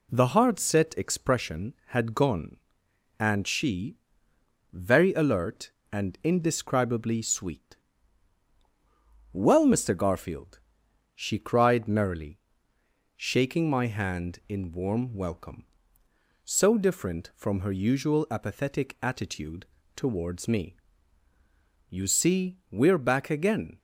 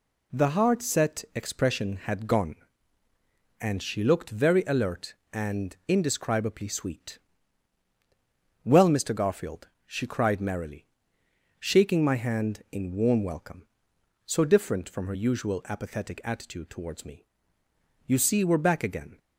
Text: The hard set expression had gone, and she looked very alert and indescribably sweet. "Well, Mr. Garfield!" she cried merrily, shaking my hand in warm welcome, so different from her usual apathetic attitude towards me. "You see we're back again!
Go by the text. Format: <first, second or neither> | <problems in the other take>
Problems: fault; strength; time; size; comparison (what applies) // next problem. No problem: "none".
second | skips "looked"; at 4.3 s // pauses between "attitude" and "towards"; slight; at 19.6 s; 0.28 s long